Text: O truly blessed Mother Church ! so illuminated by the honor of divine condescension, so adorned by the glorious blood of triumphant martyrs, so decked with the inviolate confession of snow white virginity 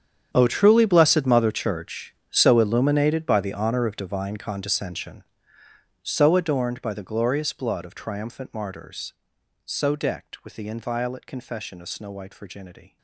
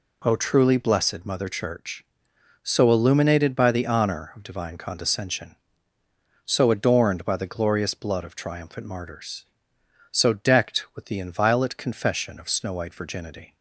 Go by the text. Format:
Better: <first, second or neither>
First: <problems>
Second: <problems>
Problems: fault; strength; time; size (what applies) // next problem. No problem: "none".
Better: second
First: gets quieter; strong; throughout; 17.5 dB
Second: none